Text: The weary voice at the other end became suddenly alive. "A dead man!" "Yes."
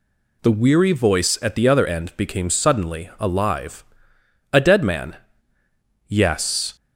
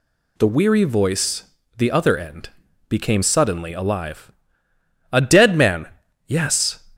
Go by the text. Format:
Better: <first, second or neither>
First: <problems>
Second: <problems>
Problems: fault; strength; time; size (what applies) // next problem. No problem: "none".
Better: first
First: none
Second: skips "at"; at 1.6 s // pauses between "end" and "became"; at 2.4 s; 0.40 s long